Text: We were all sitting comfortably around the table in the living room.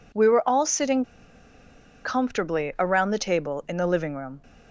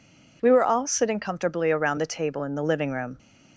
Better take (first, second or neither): second